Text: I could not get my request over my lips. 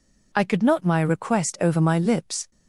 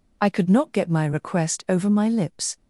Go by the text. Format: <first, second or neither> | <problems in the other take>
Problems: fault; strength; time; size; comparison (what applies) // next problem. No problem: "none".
second | skips "get"; at 0.8 s